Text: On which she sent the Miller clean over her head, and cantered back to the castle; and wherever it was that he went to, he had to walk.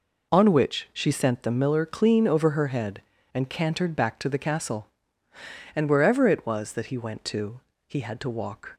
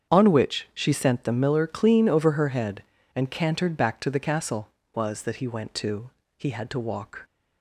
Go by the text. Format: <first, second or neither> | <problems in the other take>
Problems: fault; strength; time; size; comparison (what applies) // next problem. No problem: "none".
first | starts louder than the rest; strong; until 1.1 s; 7.5 dB // skips "and wherever it"; at 4.8 s